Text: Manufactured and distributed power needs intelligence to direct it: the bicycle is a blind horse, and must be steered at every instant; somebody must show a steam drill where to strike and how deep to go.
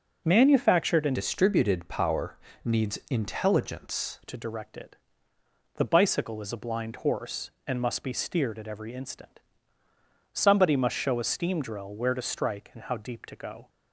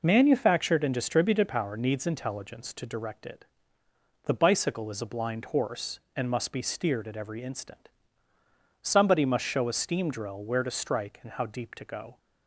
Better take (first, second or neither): second